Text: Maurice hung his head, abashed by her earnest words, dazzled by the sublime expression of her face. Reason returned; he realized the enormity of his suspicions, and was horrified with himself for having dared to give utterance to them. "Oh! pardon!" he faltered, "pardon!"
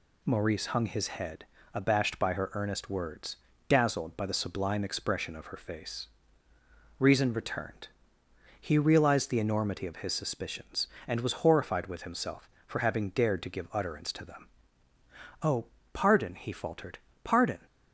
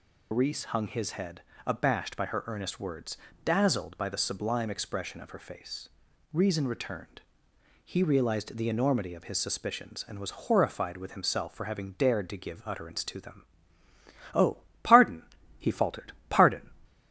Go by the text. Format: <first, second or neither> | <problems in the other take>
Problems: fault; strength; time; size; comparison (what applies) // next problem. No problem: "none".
first | loses the start of "Maurice"; at 0.3 s; 105 ms